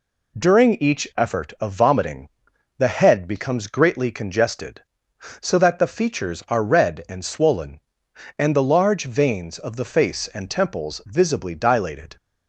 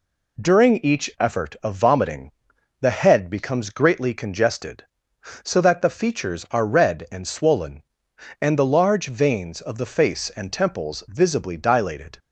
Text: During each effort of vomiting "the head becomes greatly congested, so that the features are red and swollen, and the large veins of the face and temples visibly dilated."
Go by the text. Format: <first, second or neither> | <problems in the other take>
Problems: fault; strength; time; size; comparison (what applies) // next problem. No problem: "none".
neither | pauses between "vomiting" and "the"; noticeable; the same in both